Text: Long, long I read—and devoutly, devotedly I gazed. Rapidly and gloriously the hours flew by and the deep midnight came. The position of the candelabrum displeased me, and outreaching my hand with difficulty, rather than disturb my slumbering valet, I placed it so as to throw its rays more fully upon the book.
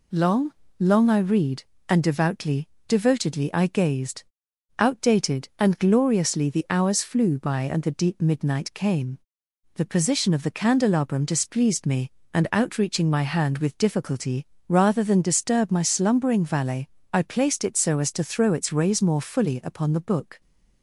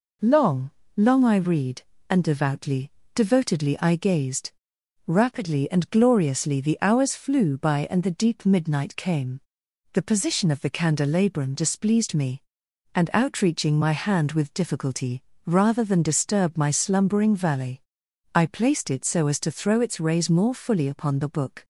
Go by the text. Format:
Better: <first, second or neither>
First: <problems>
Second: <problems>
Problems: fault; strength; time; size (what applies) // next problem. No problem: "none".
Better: second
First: says "Outdated" for "Rapidly"; at 4.7 s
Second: none